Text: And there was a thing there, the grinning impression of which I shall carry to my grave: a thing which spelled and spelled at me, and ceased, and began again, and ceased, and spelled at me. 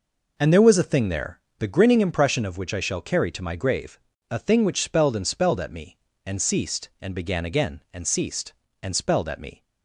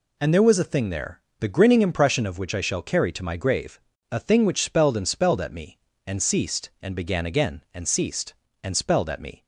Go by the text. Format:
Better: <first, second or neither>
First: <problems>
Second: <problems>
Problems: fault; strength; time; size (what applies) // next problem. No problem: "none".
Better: second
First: starts louder than the rest; noticeable; until 1.4 s; 5 dB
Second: none